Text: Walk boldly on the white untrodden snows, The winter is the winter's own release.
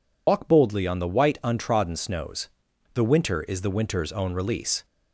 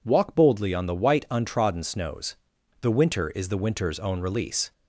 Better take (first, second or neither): second